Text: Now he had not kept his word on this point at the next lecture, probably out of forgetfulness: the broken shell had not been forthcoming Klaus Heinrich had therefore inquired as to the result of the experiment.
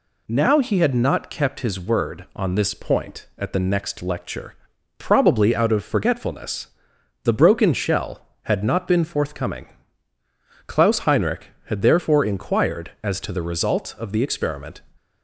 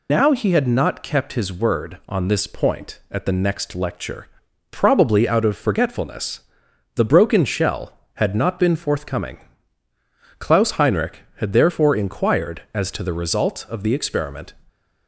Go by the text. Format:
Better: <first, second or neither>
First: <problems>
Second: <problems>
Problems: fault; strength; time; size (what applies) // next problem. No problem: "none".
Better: first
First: pauses between "forthcoming" and "Klaus"; at 9.6 s; 1.0 s long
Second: loses the start of "Now"; at 0.0 s; 95 ms // pauses between "forthcoming" and "Klaus"; at 9.3 s; 1.0 s long